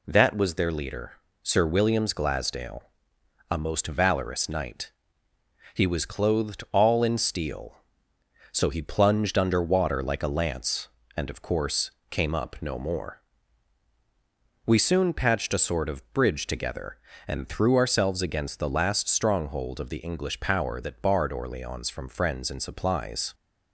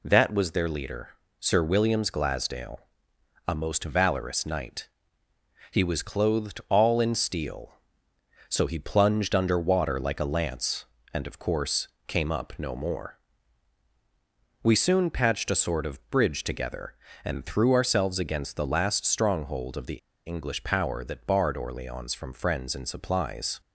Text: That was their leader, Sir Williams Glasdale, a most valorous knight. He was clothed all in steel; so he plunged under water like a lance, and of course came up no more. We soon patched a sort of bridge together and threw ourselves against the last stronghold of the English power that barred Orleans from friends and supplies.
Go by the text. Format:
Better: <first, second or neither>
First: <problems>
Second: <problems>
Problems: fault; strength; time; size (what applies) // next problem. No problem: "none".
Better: first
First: pauses between "course" and "came"; slight; at 11.8 s; 0.22 s long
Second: pauses between "course" and "came"; slight; at 11.8 s; 0.22 s long // pauses between "the" and "English"; slight; at 19.9 s; 0.28 s long